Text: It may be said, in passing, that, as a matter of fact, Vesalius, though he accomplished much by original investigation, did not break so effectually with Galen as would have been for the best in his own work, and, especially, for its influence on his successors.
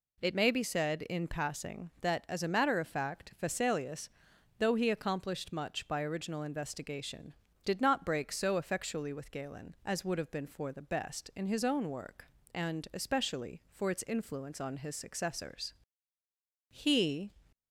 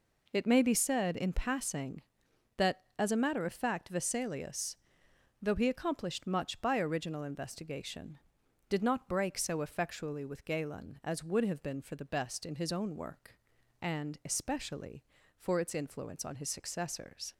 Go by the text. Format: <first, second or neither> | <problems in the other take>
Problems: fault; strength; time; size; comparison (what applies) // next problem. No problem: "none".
second | goes on to say "He"; noticeable; from 16.6 s on; 0.62 s long